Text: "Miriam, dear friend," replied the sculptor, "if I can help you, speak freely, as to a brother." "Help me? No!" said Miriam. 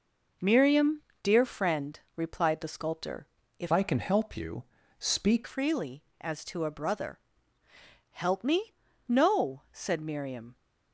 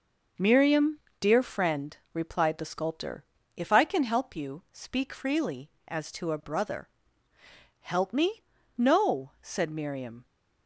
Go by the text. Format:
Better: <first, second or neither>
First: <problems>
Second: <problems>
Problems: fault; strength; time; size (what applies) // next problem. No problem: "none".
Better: second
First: changes voice from "I" to "speak"; from 3.7 to 5.4 s; 1.7 s long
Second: none